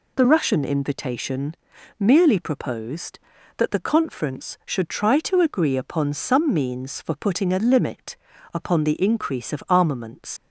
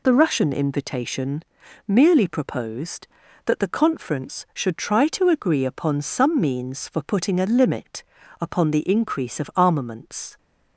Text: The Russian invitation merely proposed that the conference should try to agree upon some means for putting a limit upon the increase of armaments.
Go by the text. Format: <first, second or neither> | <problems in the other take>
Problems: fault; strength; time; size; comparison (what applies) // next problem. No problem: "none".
second | pauses between "invitation" and "merely"; at 1.5 s; 0.42 s long; also in the second // pauses between "limit" and "upon"; slight; at 8.1 s; 0.36 s long; slight in the second // leaves "armaments" unfinished; at 10.3 s; 135 ms